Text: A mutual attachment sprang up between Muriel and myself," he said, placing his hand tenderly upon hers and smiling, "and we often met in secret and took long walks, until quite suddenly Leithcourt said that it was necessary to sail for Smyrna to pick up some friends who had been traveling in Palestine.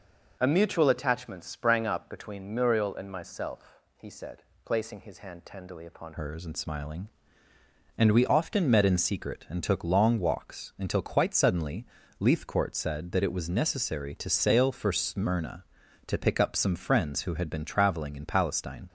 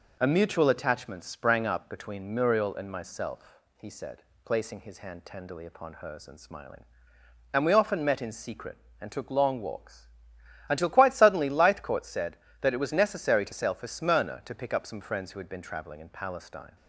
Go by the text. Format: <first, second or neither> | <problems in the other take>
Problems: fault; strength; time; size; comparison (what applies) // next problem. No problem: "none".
second | changes voice at "hers"; from 6.1 s on; 12.7 s long // pauses between "suddenly" and "Leithcourt"; slight; at 11.8 s; 0.32 s long